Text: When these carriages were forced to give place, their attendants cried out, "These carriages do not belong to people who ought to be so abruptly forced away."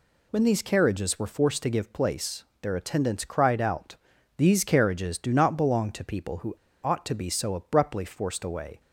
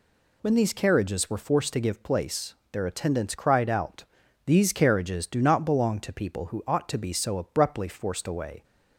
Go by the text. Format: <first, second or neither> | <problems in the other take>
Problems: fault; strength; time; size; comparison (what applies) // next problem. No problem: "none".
second | pauses between "who" and "ought"; slight; at 6.5 s; 0.31 s long